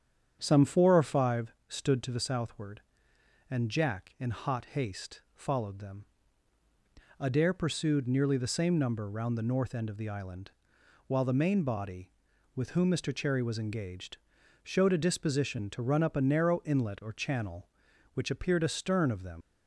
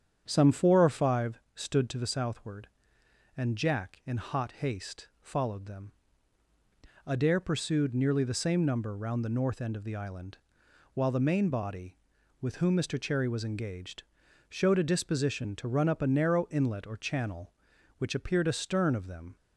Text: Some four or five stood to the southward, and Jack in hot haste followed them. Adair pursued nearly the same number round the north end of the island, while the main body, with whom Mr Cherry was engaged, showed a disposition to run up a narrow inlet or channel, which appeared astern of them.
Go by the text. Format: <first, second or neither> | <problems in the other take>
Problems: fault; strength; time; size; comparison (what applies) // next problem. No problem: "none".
second | starts louder than the rest; strong; until 1.4 s; 8.5 dB; strong in the second // pauses between "five" and "stood"; slight; at 1.5 s; 0.16 s long; slight in the second // pauses between "haste" and "followed"; slight; at 5.1 s; 0.16 s long; slight in the second // leaves "them" unfinished; at 19.4 s; 105 ms